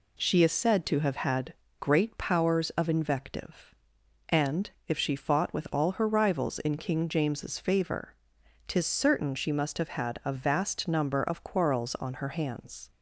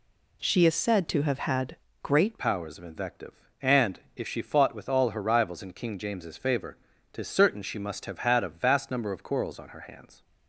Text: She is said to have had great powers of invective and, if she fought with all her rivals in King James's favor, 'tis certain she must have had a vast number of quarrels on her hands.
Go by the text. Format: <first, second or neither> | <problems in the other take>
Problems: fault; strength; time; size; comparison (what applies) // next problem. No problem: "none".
first | pauses between "had" and "great"; slight; at 1.7 s; 0.26 s long; slight in the first // changes voice at "powers"; from 2.3 s on; 7.9 s long